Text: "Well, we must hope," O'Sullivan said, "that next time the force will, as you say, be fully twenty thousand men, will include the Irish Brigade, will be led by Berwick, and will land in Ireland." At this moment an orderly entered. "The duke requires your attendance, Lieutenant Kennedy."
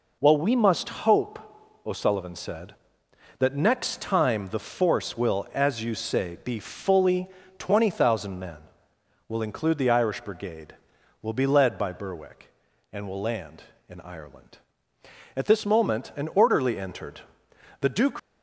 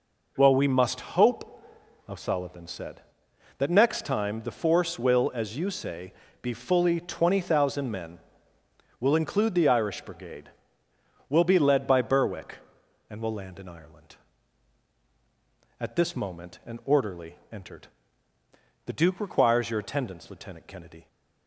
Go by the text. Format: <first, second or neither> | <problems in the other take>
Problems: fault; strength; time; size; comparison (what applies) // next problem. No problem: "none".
second | pauses between "fully" and "twenty"; slight; at 7.2 s; 0.30 s long // stops before "requires your attendance Lieutenant Kennedy"; at 18.1 s